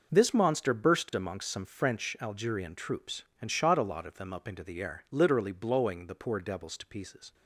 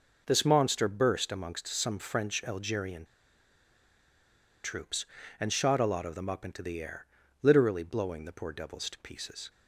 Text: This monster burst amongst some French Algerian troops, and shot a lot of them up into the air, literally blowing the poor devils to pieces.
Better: first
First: none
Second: pauses between "Algerian" and "troops"; strong; at 3.0 s; 1.5 s long

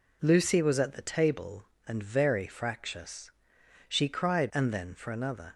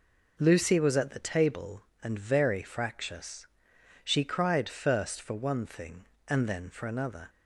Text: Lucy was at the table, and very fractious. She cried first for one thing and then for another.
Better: second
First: skips "first for one thing"; at 4.5 s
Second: none

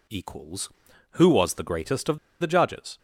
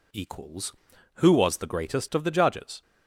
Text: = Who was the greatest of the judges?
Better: second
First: pauses between "of" and "the"; slight; at 2.1 s; 0.23 s long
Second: none

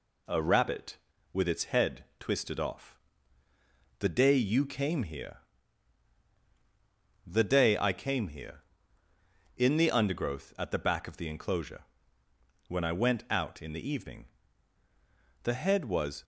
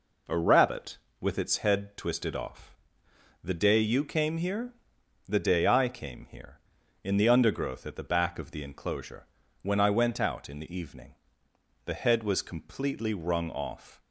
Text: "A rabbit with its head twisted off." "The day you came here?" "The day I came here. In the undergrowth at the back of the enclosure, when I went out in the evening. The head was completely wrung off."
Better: second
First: stops before "completely wrung off"; at 16.2 s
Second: none

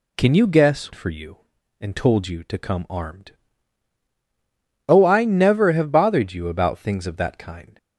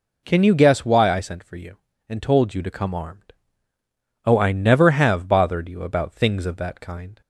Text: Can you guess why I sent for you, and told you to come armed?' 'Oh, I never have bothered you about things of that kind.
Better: second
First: skips "why I sent"; at 0.9 s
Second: none

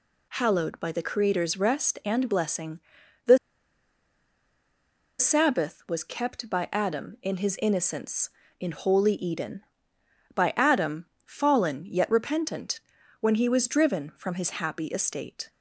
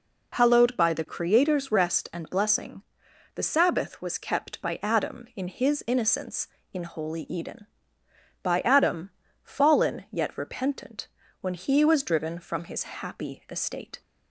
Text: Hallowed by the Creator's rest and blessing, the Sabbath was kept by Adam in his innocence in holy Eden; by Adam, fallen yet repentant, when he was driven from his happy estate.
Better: second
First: pauses between "the" and "Sabbath"; strong; at 3.3 s; 1.8 s long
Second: none

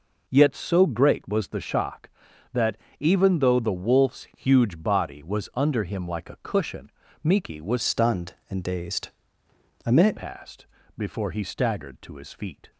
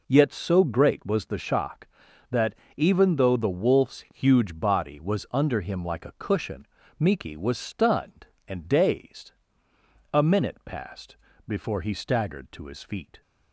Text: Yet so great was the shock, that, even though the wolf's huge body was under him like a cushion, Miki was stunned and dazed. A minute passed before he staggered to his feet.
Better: second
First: changes voice from "stunned" to "minute"; from 7.8 to 10.1 s; 2.3 s long // pauses between "passed" and "before"; slight; at 10.6 s; 0.30 s long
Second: pauses between "passed" and "before"; slight; at 11.1 s; 0.30 s long

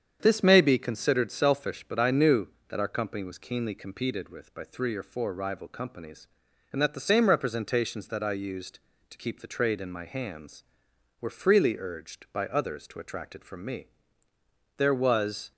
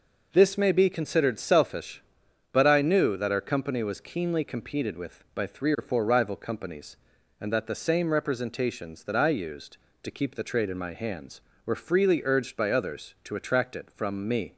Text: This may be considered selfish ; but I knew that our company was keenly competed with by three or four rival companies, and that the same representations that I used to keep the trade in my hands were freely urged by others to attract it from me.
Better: second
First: starts louder than the rest; strong; until 1.2 s; 8 dB // goes on to say "There was"; noticeable; from 14.7 s on; 0.74 s long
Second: none

